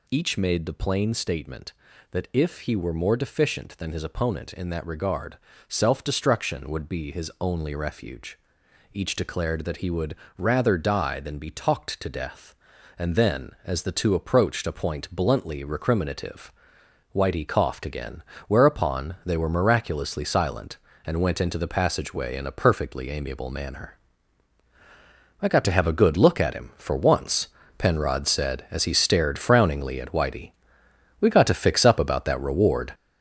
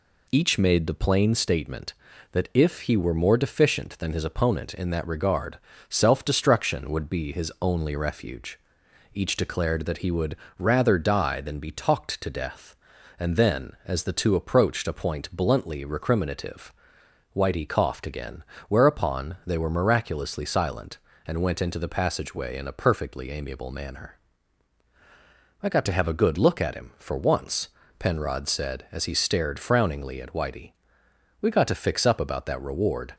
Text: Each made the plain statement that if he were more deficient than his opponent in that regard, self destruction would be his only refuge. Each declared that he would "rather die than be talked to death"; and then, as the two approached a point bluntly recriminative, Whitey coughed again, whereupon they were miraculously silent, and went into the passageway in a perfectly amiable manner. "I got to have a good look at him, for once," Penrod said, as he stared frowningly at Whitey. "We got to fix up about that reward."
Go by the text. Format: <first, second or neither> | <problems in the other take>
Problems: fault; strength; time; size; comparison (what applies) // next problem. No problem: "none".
second | gets louder; throughout; 7 dB // pauses between "would" and "rather"; slight; at 10.1 s; 0.22 s long; slight in the second